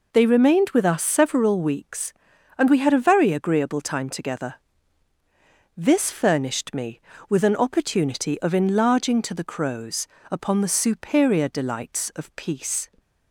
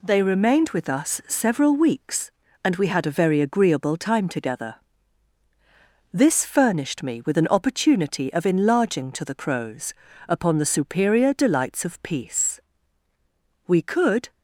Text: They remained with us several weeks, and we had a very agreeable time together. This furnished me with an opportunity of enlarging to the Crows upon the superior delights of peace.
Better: first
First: pauses between "Crows" and "upon"; slight; at 10.0 s; 0.24 s long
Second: pauses between "Crows" and "upon"; slight; at 9.9 s; 0.36 s long // goes on to say "We could"; noticeable; from 13.6 s on; 0.64 s long

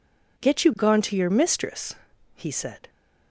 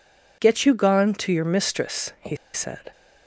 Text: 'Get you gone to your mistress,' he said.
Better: first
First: none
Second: pauses between "he" and "said"; slight; at 2.3 s; 0.17 s long

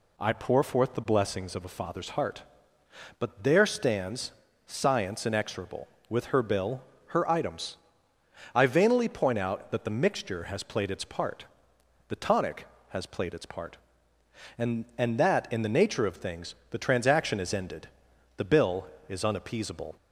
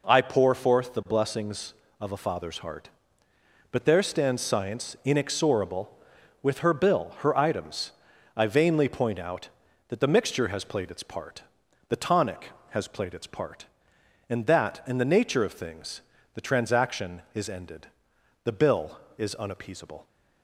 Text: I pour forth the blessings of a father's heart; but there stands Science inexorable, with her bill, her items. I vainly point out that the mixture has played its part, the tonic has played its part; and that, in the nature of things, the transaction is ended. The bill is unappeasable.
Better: second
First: pauses between "stands" and "Science"; slight; at 4.3 s; 0.34 s long // says "and" twice; at 14.9 s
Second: none

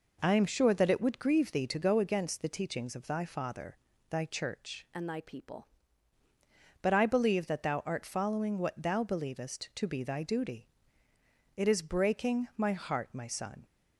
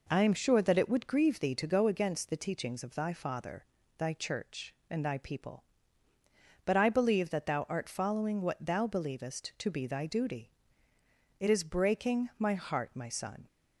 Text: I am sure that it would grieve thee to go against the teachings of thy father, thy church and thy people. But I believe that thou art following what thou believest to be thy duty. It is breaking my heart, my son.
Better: second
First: changes voice from "and" to "people"; from 4.9 to 5.6 s; 0.7 s long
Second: none

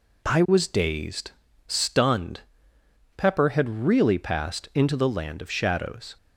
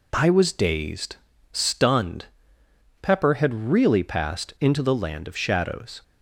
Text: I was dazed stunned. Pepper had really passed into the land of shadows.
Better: neither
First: pauses between "dazed" and "stunned"; slight; at 1.3 s; 0.36 s long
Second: pauses between "dazed" and "stunned"; slight; at 1.1 s; 0.36 s long

